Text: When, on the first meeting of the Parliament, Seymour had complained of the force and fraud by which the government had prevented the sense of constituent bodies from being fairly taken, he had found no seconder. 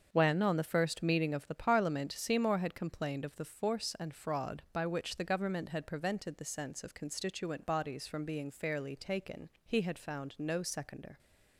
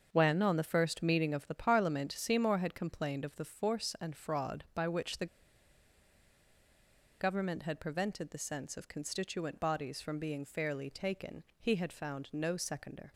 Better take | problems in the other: first | starts louder than the rest; until 1.1 s; 7 dB; also in the first // pauses between "the" and "government"; strong; at 5.2 s; 1.9 s long

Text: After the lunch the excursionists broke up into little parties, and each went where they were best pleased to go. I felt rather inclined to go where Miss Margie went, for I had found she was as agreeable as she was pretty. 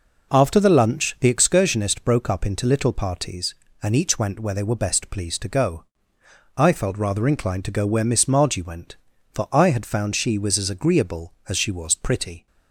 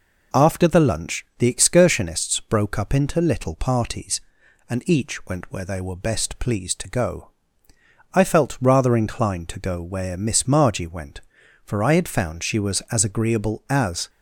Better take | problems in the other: first | stops before "she was pretty"; at 14.0 s

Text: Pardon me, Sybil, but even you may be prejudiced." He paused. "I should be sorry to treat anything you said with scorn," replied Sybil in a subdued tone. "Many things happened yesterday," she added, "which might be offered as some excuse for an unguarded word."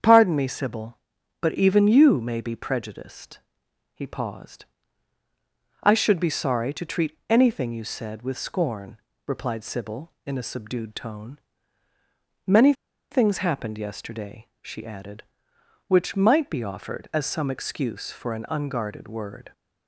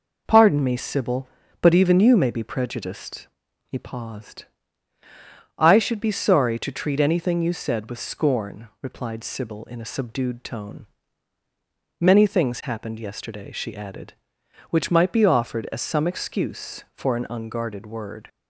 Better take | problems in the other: second | starts louder than the rest; strong; until 1.4 s; 8 dB // pauses between "Many" and "things"; at 12.7 s; 0.38 s long

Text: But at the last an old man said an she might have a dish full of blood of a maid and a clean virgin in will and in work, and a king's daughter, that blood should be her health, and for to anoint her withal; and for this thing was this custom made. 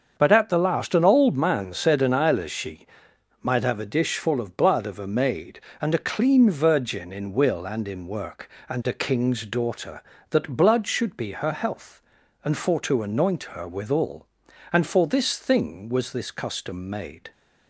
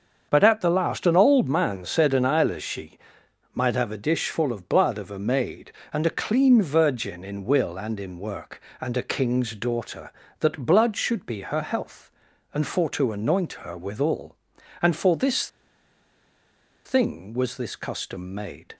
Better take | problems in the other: first | starts louder than the rest; until 1.3 s; 7 dB; also in the first // pauses between "she" and "might"; noticeable; at 2.9 s; 0.56 s long; noticeable in the first // pauses between "this" and "thing"; strong; at 15.4 s; 1.3 s long

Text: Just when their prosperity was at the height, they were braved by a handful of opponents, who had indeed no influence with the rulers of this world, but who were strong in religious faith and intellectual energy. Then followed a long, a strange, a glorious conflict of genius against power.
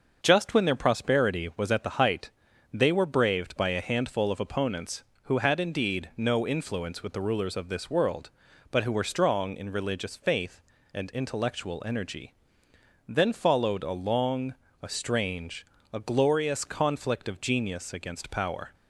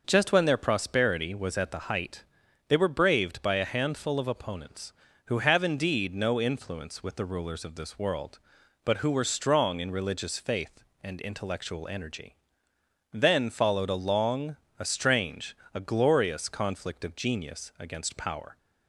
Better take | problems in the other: first | starts louder than the rest; noticeable; until 1.0 s; 6 dB; also in the first // says "have" for "had"; at 5.3 s

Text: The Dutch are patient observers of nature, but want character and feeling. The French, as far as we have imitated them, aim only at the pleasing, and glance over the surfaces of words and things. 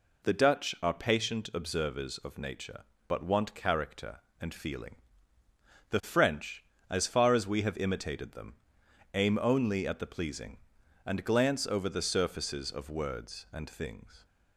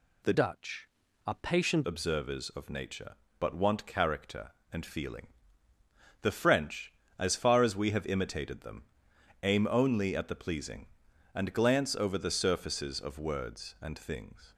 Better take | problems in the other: first | changes voice from "Dutch" to "patient"; from 0.3 to 1.8 s; 1.5 s long

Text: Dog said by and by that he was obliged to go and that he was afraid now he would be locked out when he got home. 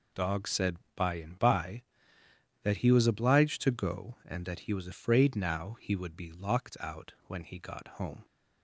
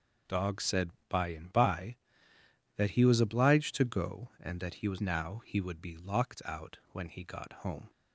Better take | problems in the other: first | skips "afraid"; at 4.9 s

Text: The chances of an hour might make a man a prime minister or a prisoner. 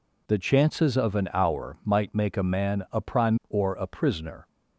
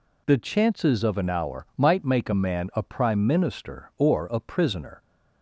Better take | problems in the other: second | skips "minister"; at 3.4 s

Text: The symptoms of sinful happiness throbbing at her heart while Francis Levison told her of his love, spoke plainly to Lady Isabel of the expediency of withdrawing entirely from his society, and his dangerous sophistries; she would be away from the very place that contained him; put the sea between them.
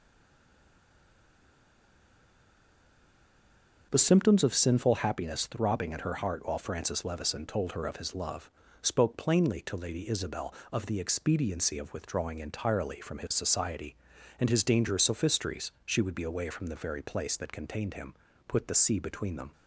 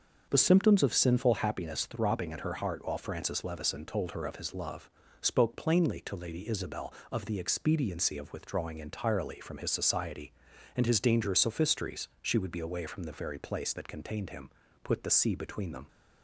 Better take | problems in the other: second | stays silent before the first word; strong; until 3.9 s; 3.9 s long // starts louder than the rest; until 4.9 s; 6.5 dB; also in the second

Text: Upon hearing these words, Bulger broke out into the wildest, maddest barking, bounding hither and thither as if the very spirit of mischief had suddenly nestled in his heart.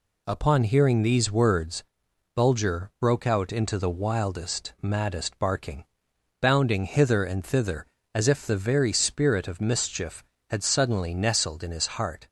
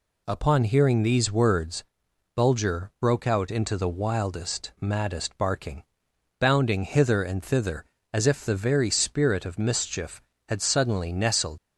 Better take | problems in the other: first | stops before "in his heart"; at 11.5 s

